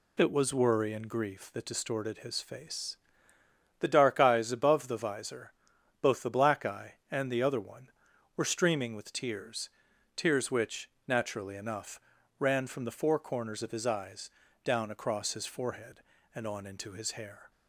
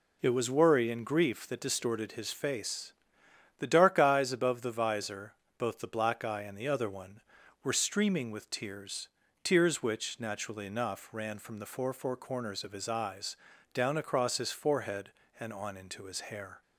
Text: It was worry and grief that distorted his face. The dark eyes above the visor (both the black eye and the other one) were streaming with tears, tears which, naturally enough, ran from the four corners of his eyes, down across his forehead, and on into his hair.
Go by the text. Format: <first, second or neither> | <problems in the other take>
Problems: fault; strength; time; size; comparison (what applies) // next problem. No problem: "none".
first | says "four" twice; at 11.9 s